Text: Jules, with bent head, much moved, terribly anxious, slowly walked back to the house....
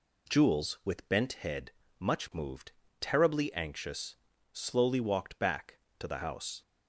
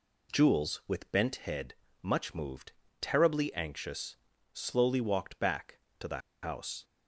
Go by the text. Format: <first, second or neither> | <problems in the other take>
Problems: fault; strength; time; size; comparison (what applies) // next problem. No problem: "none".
first | pauses between "the" and "house"; slight; at 6.1 s; 0.24 s long